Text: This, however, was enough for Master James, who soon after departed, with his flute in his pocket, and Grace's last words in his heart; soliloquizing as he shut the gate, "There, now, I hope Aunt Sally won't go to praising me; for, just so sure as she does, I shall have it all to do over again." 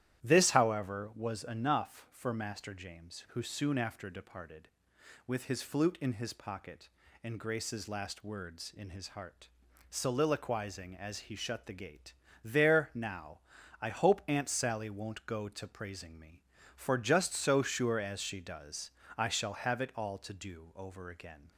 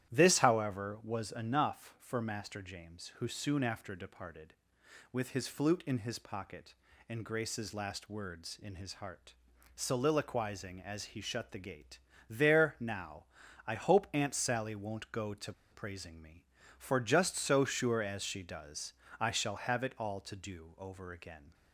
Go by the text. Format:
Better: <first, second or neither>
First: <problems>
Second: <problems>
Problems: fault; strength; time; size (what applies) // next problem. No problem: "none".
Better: first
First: starts louder than the rest; strong; until 1.2 s; 12 dB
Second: starts louder than the rest; strong; until 1.1 s; 12 dB // pauses between "to" and "praising"; slight; at 15.5 s; 0.18 s long